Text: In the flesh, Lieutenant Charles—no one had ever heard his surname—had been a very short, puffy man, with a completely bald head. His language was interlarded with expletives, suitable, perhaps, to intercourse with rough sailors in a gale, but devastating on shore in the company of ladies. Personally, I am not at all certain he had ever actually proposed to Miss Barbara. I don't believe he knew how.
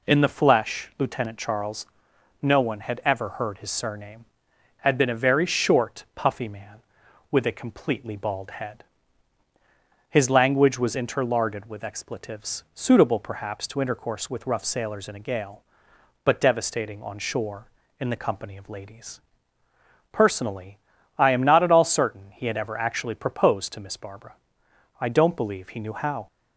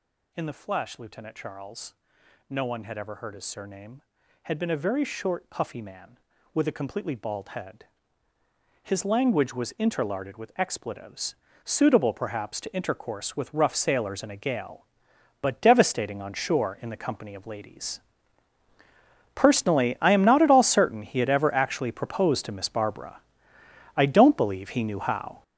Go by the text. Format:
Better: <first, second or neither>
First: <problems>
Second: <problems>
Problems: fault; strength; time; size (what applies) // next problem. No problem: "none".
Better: first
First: none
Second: gets louder; strong; throughout; 10 dB